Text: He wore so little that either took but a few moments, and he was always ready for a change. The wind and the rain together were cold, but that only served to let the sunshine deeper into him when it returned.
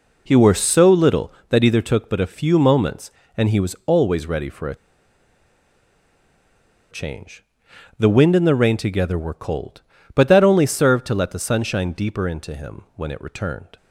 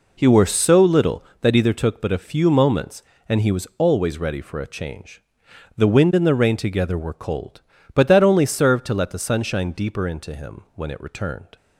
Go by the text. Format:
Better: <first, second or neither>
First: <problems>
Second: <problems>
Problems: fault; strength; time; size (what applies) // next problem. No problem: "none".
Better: second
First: pauses between "a" and "change"; strong; at 4.7 s; 2.1 s long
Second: none